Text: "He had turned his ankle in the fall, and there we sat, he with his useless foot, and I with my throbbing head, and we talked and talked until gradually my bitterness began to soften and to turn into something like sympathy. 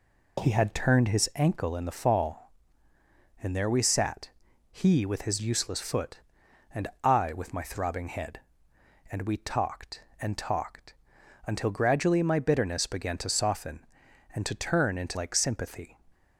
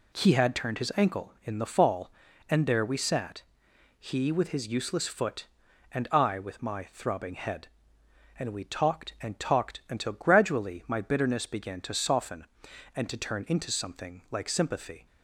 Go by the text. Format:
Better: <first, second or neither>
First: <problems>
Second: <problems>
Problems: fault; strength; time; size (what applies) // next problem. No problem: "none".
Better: second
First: pauses between "and" and "I"; slight; at 6.8 s; 0.16 s long // pauses between "talked" and "until"; noticeable; at 10.9 s; 0.50 s long // skips "something"; at 15.1 s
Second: none